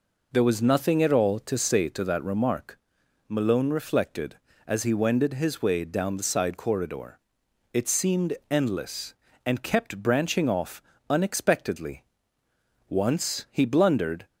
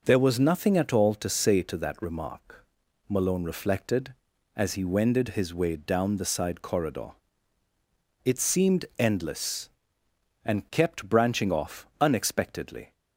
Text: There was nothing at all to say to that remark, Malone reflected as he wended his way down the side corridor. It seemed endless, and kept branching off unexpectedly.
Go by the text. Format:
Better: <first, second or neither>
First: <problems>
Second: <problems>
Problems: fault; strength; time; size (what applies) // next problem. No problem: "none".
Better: second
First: pauses between "off" and "unexpectedly"; slight; at 10.8 s; 0.26 s long // goes on to say "Once he blundered"; from 12.8 s on; 1.3 s long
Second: none